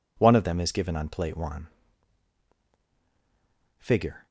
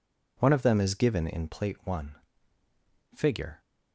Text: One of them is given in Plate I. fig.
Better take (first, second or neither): second